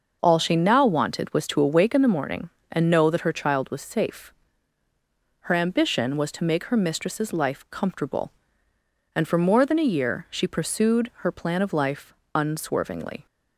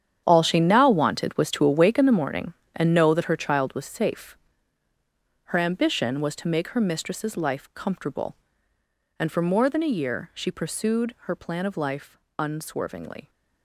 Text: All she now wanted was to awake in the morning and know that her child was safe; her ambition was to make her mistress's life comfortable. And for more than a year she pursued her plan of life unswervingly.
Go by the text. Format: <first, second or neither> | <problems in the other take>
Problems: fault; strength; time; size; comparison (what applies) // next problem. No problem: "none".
first | gets quieter; strong; throughout; 13 dB // starts louder than the rest; strong; until 1.2 s; 9 dB; noticeable in the first // pauses between "life" and "unswervingly"; slight; at 12.1 s; 0.22 s long; slight in the first